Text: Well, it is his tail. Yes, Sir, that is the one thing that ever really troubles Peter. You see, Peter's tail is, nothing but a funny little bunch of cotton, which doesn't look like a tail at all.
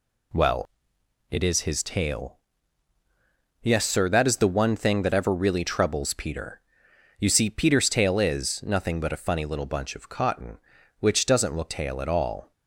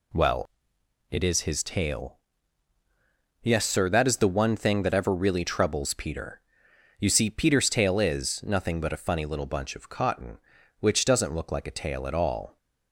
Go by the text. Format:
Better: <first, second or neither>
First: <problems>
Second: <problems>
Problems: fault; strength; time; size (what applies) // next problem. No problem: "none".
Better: second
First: skips "like a"; at 11.7 s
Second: none